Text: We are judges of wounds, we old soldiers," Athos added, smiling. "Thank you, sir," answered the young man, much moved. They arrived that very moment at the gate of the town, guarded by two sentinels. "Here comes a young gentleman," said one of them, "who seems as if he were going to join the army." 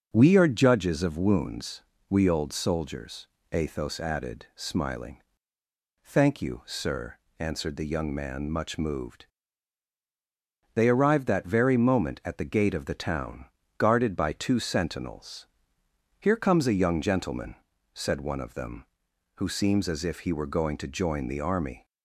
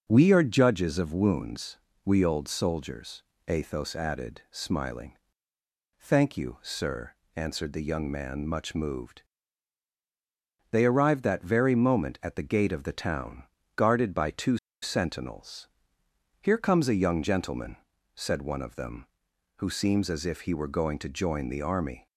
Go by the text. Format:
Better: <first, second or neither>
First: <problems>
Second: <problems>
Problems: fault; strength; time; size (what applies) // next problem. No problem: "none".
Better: first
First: starts louder than the rest; until 1.1 s; 6 dB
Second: starts louder than the rest; until 1.0 s; 6 dB // pauses between "two" and "sentinels"; slight; at 14.5 s; 0.25 s long